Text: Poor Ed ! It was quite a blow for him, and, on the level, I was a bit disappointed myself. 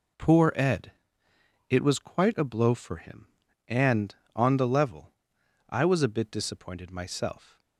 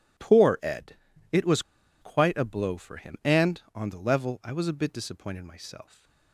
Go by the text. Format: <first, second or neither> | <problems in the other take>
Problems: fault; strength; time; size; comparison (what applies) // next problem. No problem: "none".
first | pauses between "was" and "quite"; at 1.6 s; 0.39 s long // stays silent after the last word; slight; from 5.8 s on; 0.5 s long